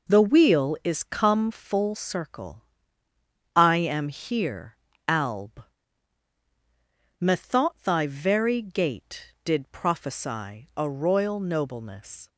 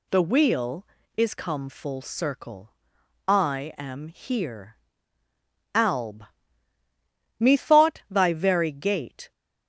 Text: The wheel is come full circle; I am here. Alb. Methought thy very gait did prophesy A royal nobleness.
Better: first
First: none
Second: stops before "did prophesy A royal nobleness"; at 9.3 s

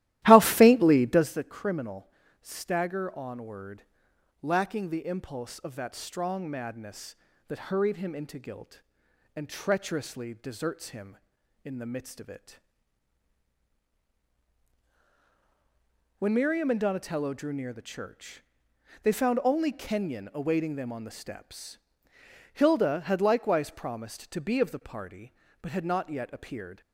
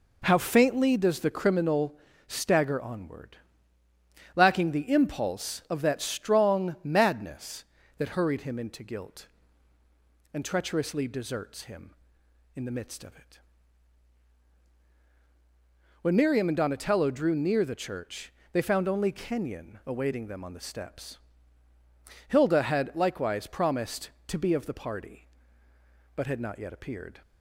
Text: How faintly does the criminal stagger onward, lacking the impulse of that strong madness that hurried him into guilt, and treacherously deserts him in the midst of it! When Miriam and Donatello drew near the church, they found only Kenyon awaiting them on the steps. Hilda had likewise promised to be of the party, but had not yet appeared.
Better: second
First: starts louder than the rest; strong; until 1.4 s; 15 dB // pauses between "criminal" and "stagger"; slight; at 2.0 s; 0.34 s long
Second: pauses between "criminal" and "stagger"; slight; at 1.9 s; 0.30 s long

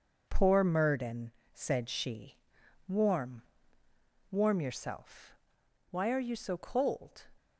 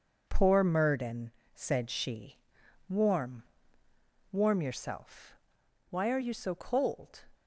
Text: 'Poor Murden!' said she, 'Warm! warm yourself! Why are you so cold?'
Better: neither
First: none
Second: none

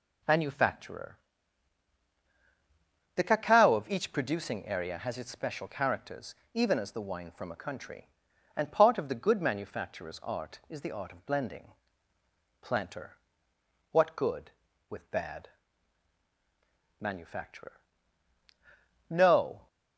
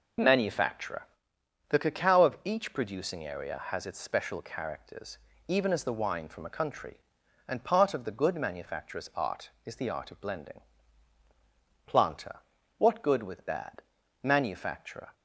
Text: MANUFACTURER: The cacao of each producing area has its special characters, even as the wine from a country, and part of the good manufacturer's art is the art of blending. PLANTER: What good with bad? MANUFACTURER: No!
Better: first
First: none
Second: stops before "No"; at 15.1 s

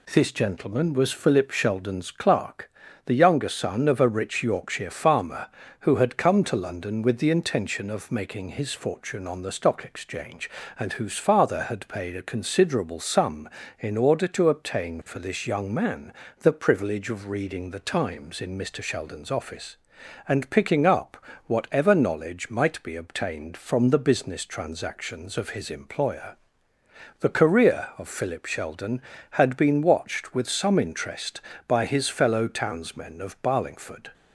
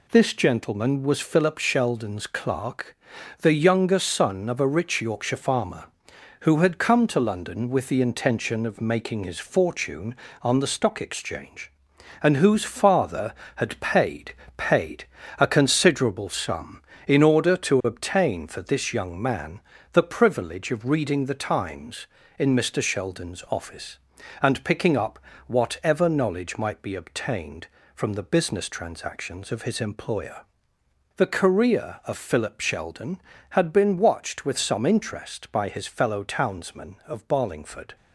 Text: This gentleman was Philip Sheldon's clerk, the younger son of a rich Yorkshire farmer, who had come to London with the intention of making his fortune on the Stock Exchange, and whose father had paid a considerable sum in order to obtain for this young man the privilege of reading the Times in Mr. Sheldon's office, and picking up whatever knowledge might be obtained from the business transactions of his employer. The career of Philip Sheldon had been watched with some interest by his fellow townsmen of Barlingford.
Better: first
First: pauses between "man" and "the"; slight; at 16.1 s; 0.28 s long // pauses between "up" and "whatever"; slight; at 21.1 s; 0.30 s long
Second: says "paid" twice; at 14.5 s // pauses between "man" and "the"; slight; at 19.6 s; 0.32 s long // pauses between "up" and "whatever"; slight; at 25.1 s; 0.26 s long

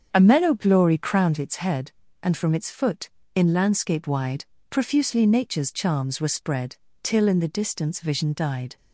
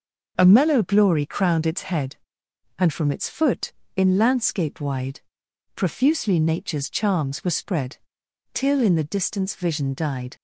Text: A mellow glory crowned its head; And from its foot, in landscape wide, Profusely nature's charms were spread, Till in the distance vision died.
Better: second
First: starts louder than the rest; strong; until 1.3 s; 7.5 dB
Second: none

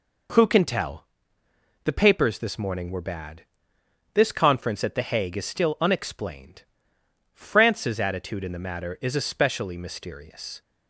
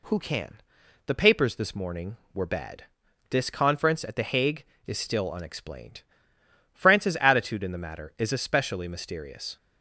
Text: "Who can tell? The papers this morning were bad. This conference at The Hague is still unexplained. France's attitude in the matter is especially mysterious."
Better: first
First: none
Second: skips "tell"; at 0.8 s

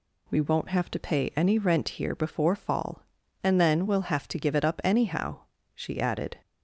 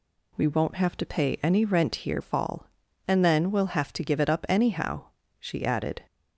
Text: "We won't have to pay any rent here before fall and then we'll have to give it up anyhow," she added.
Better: first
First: none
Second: skips "before"; at 2.2 s

